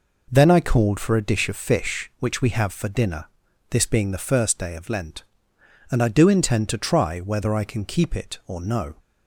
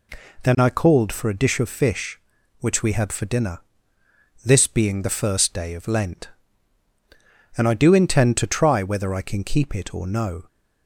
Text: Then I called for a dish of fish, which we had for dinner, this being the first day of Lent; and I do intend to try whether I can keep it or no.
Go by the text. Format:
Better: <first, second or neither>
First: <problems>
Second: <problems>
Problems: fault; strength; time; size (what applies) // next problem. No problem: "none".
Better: second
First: says "have" for "had"; at 2.5 s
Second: none